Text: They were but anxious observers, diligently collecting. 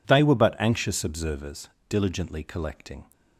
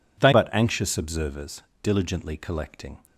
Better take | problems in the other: first | skips "were"; at 0.3 s

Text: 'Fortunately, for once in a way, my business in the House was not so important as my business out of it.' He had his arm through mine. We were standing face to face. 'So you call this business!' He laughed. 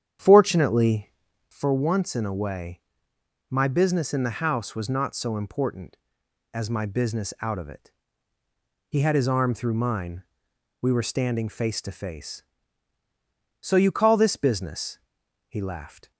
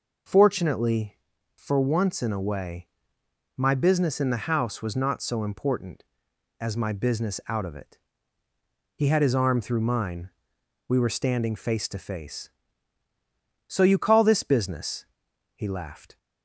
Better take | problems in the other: second | starts louder than the rest; strong; until 1.6 s; 9 dB

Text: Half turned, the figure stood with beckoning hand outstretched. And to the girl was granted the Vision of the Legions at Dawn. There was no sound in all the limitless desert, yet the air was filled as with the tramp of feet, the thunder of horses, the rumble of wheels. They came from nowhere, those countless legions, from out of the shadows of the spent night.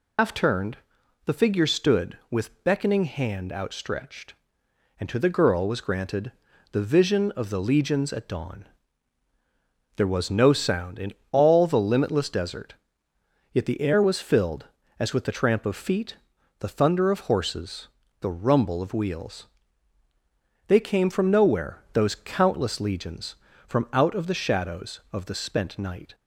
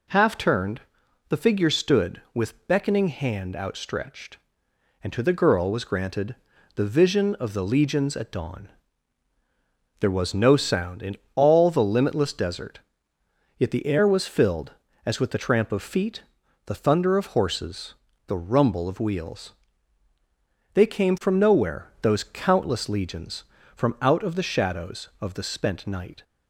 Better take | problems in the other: second | loses the start of "Half"; at 0.1 s; 135 ms // pauses between "granted" and "the"; at 6.3 s; 0.40 s long; also in the second // pauses between "in" and "all"; slight; at 11.1 s; 0.18 s long; slight in the second

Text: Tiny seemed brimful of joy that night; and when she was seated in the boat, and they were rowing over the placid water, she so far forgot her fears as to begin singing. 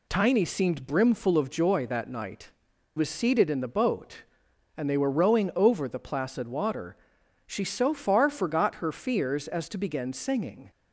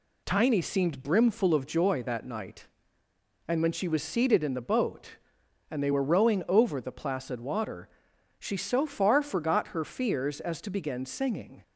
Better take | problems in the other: second | skips "and when she"; at 2.7 s

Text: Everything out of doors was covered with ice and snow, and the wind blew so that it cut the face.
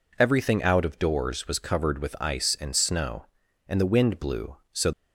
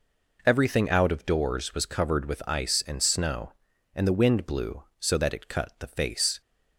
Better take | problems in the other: second | stops before "that it cut the face"; at 4.9 s

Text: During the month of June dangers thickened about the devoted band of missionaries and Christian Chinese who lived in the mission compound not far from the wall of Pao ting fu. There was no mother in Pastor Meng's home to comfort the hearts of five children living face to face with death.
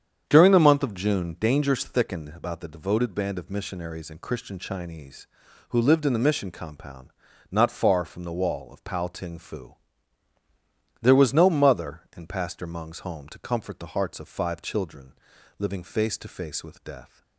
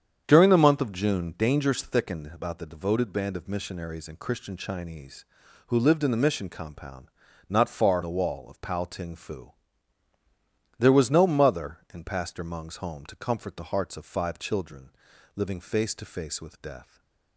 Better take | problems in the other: first | starts louder than the rest; strong; until 1.2 s; 8 dB; strong in the first // pauses between "compound" and "not"; at 7.0 s; 0.38 s long; also in the first // skips "from"; at 8.0 s // pauses between "children" and "living"; noticeable; at 14.8 s; 0.46 s long; noticeable in the first // stays silent after the last word; slight; from 16.8 s on; 0.5 s long

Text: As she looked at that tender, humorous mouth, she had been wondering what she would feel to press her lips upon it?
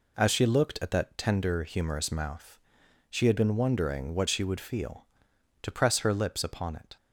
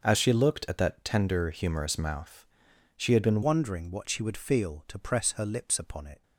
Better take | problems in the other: first | starts louder than the rest; noticeable; until 1.0 s; 6 dB // changes voice at "wondering"; from 3.4 s on; 2.8 s long

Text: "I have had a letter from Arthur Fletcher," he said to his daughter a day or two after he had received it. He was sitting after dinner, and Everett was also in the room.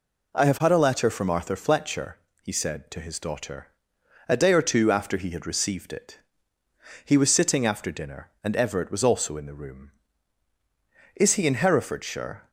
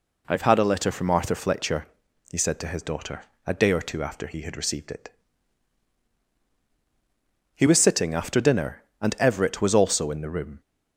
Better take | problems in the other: second | pauses between "daughter" and "a"; noticeable; at 3.6 s; 0.60 s long; slight in the second // goes on to say "Is he in Herefordshire"; from 11.1 s on; 1.3 s long

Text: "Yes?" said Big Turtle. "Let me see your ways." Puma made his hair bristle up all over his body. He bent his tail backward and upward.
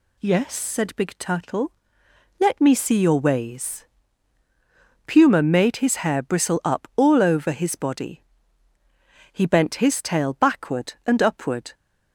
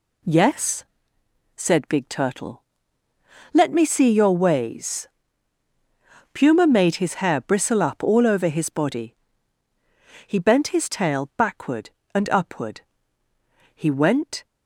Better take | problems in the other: first | goes on to say "He went"; noticeable; from 13.7 s on; 0.68 s long

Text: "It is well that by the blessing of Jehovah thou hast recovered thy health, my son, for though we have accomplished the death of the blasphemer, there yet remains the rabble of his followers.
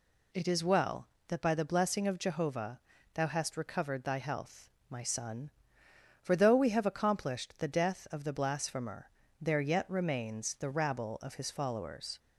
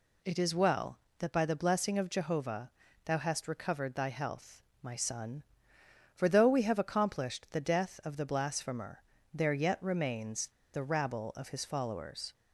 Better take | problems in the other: first | pauses between "Jehovah" and "thou"; slight; at 2.6 s; 0.36 s long; slight in the first // pauses between "remains" and "the"; slight; at 10.4 s; 0.27 s long

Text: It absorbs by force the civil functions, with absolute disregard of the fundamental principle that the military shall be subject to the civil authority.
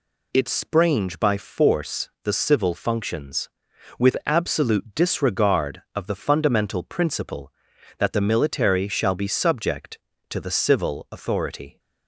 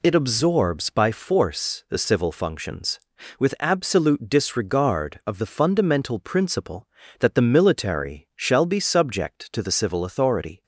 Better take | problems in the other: second | says "sprange" for "absorbs"; at 0.4 s // pauses between "force" and "the"; slight; at 2.0 s; 0.16 s long

